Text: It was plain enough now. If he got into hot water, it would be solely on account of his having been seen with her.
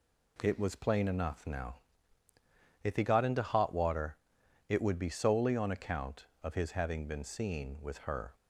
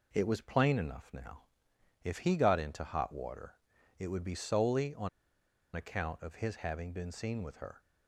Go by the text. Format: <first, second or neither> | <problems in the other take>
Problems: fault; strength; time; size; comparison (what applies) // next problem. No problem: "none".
first | pauses between "on" and "account"; noticeable; at 5.0 s; 0.66 s long